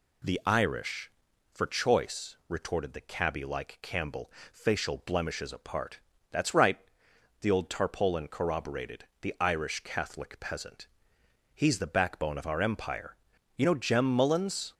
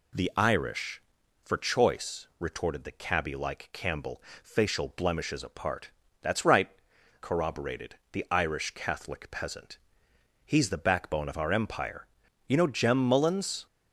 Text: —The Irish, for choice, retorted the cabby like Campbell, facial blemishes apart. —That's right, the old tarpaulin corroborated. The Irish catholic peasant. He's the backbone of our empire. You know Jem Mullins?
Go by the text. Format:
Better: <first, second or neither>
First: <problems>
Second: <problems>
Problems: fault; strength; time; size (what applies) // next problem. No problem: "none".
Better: first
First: none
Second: skips "the old tarpaulin"; at 6.9 s